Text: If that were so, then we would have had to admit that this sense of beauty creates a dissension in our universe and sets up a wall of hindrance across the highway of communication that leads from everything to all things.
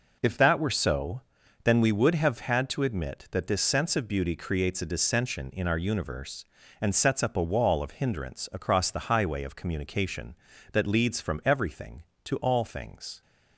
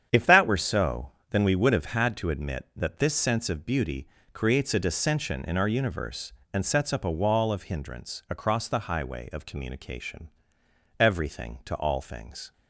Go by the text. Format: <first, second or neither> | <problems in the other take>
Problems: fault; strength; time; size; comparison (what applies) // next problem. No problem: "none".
first | starts louder than the rest; strong; until 1.1 s; 8.5 dB // pauses between "beauty" and "creates"; slight; at 4.0 s; 0.24 s long // skips "that leads from"; at 10.6 s